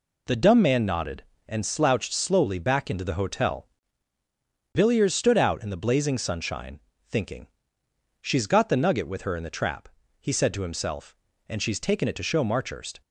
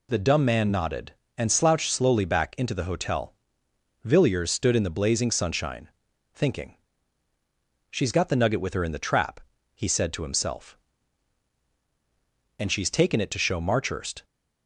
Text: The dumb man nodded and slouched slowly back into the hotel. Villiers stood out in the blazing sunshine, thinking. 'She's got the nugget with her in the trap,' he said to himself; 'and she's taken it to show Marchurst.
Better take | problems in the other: first | skips "out"; at 4.7 s

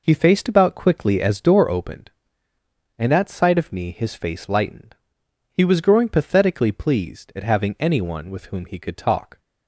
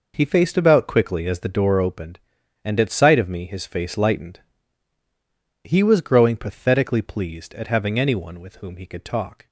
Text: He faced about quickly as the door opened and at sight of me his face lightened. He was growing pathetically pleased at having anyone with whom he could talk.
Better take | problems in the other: second | skips "the"; at 1.4 s

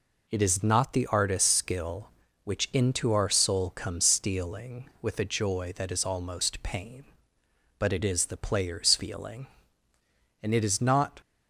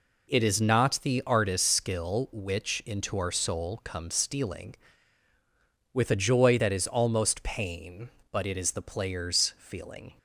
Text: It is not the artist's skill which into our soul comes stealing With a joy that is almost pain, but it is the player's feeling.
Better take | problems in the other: second | goes on to say "And it is not"; noticeable; from 10.4 s on; 0.78 s long

